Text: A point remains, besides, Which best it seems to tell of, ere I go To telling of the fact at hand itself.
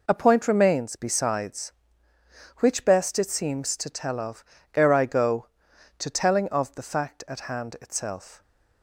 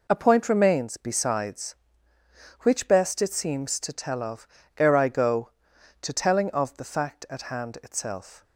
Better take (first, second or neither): neither